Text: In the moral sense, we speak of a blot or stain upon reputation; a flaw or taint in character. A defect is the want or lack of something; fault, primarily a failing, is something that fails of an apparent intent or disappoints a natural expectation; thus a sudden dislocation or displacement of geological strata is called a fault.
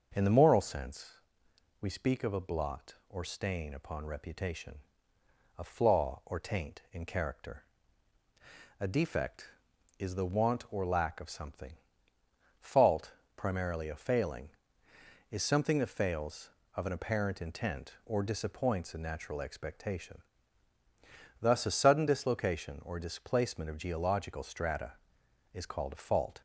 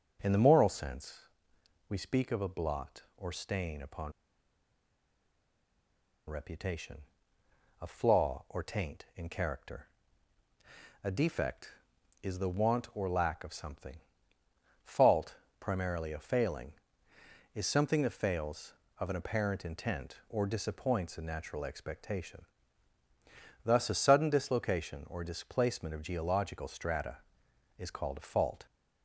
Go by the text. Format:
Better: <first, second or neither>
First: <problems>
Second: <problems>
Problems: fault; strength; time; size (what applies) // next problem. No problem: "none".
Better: first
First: starts louder than the rest; until 1.8 s; 6.5 dB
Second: starts louder than the rest; until 1.9 s; 6.5 dB // pauses between "upon" and "reputation"; strong; at 4.1 s; 2.1 s long